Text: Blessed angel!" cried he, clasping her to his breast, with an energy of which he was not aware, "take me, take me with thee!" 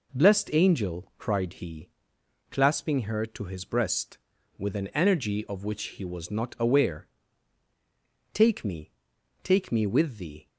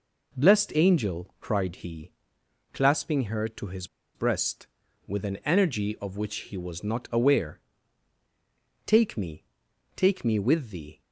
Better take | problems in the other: first | pauses between "his" and "breast"; slight; at 3.8 s; 0.29 s long

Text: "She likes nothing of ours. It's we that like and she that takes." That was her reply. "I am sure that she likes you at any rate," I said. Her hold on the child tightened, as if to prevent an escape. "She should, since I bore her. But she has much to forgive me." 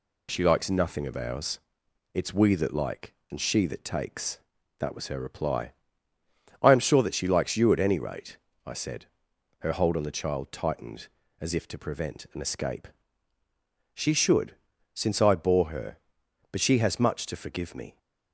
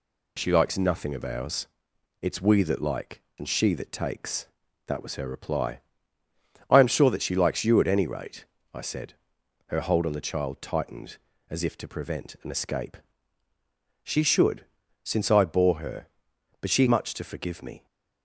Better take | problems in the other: first | skips "has"; at 16.8 s

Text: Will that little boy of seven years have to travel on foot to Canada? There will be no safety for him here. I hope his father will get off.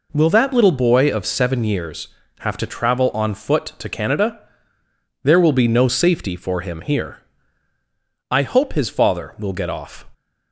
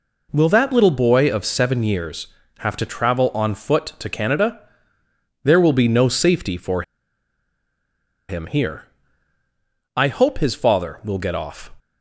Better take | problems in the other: first | pauses between "for" and "him"; strong; at 6.8 s; 1.4 s long

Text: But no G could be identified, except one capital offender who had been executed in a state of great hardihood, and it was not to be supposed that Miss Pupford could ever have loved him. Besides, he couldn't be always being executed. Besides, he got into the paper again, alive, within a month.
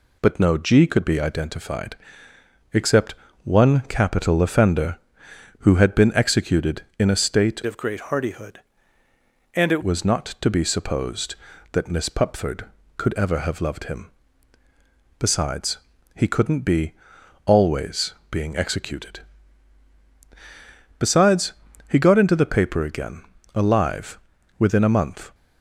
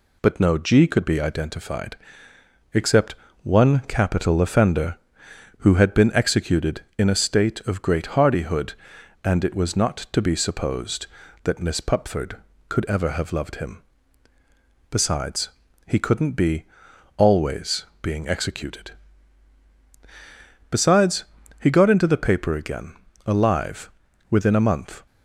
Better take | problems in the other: second | pauses between "except" and "one"; slight; at 3.1 s; 0.30 s long; slight in the second // changes voice from "of" to "it"; from 7.6 to 9.8 s; 2.2 s long // pauses between "be" and "always"; noticeable; at 16.9 s; 0.54 s long; noticeable in the second // pauses between "always" and "being"; slight; at 18.1 s; 0.16 s long; slight in the second

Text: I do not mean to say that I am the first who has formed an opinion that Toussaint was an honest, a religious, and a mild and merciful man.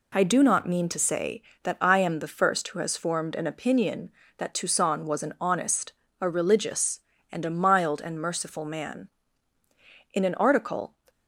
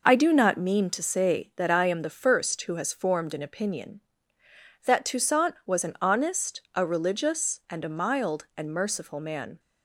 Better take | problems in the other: second | goes on to say "In an article"; noticeable; from 10.1 s on; 0.80 s long

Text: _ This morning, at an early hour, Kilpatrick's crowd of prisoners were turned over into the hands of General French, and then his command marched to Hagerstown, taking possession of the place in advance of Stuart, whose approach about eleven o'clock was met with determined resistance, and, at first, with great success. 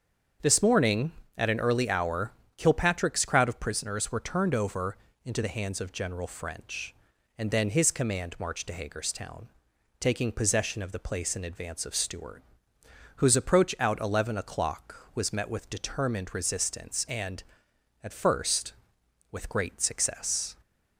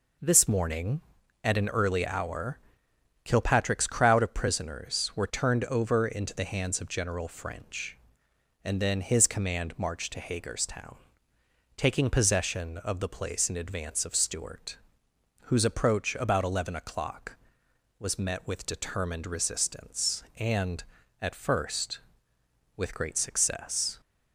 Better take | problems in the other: second | starts louder than the rest; strong; until 1.6 s; 7 dB // pauses between "over" and "into"; slight; at 4.9 s; 0.26 s long // says "out" for "about"; at 13.7 s

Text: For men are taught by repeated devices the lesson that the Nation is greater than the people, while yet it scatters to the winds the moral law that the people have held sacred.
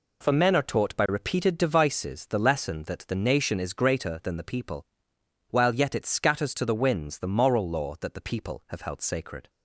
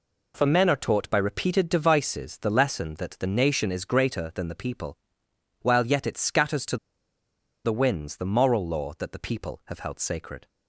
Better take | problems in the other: first | pauses between "to" and "the"; noticeable; at 6.7 s; 0.87 s long

